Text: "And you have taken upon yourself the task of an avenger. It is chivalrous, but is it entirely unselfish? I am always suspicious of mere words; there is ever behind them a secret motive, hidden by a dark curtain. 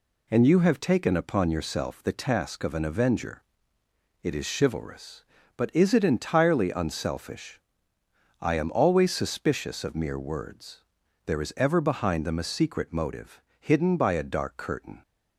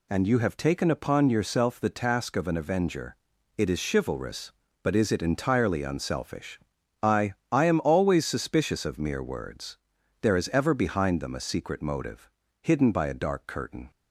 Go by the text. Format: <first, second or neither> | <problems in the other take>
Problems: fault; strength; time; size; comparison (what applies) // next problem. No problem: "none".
first | says "I" twice; at 7.5 s